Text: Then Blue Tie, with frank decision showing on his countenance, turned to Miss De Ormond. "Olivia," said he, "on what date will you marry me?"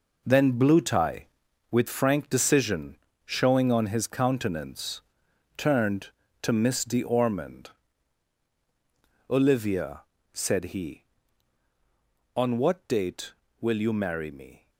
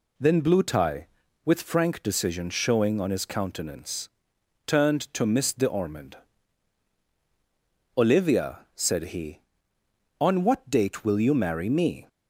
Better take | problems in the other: second | gets quieter; strong; throughout; 10.5 dB // pauses between "decision" and "showing"; slight; at 2.9 s; 0.30 s long

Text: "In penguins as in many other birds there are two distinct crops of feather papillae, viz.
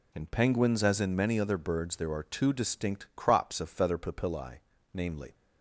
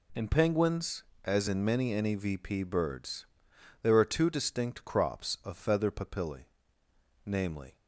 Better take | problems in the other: first | says "nevp" for "other"; at 1.9 s // pauses between "birds" and "there"; noticeable; at 3.2 s; 0.56 s long

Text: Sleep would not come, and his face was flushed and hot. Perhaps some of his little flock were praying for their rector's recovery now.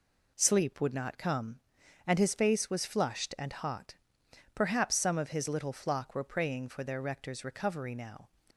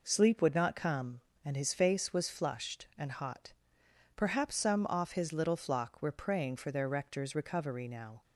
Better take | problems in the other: first | says "off" for "of"; at 4.8 s

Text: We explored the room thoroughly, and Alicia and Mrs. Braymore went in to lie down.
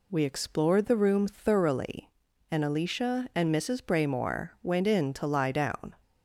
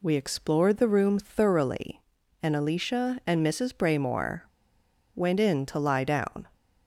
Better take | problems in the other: first | pauses between "Braymore" and "went"; noticeable; at 4.4 s; 0.73 s long

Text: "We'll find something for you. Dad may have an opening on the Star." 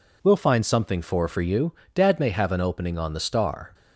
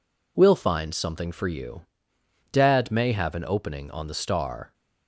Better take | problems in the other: second | says "for" twice; at 1.2 s

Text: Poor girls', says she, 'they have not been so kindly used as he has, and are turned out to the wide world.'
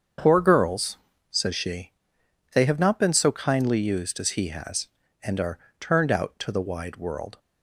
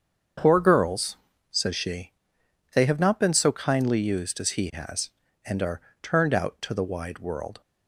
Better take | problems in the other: neither | starts louder than the rest; the same in both // pauses between "are" and "turned"; slight; the same in both

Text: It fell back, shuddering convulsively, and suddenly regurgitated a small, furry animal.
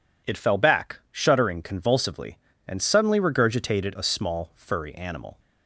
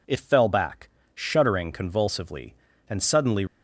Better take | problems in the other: first | stops before "regurgitated a small furry animal"; at 3.4 s

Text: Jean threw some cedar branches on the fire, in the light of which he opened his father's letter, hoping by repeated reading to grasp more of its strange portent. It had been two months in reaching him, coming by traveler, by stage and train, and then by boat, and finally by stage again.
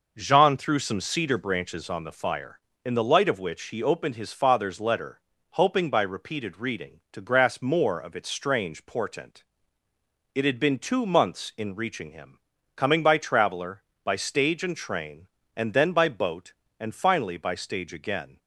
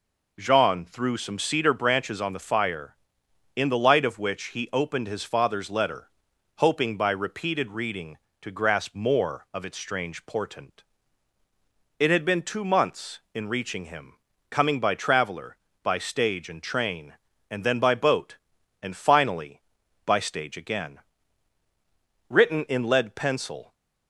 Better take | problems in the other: first | goes on to say "Written in lead pencil"; from 22.2 s on; 1.4 s long

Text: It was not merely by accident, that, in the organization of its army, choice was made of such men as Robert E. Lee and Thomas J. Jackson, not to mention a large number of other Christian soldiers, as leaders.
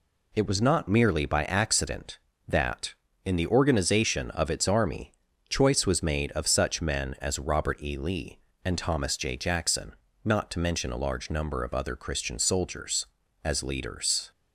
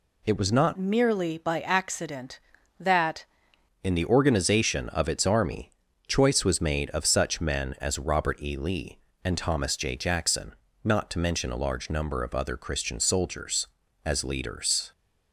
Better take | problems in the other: first | changes voice from "merely" to "that"; from 0.7 to 3.2 s; 2.5 s long

